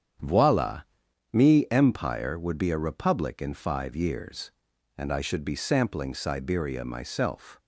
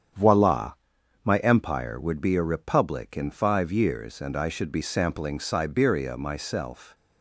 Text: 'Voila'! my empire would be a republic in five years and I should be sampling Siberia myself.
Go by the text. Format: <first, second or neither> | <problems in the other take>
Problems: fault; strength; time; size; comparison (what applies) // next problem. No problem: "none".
second | starts louder than the rest; strong; until 1.7 s; 8.5 dB; strong in the second // says "me" for "my"; at 1.3 s